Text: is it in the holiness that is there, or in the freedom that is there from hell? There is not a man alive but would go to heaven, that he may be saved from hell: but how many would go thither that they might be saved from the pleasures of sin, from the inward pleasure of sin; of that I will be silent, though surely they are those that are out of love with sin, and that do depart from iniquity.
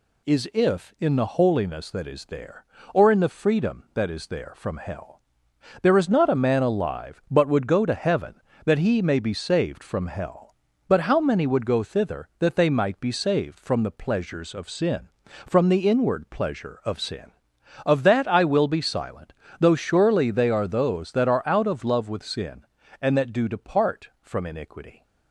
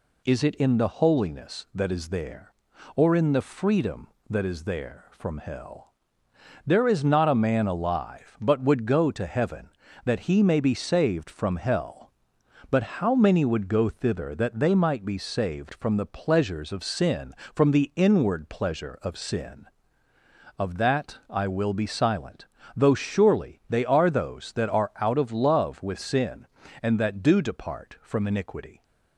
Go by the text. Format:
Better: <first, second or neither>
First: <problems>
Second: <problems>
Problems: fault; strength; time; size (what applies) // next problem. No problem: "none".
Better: second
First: says "if" for "it"; at 0.5 s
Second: none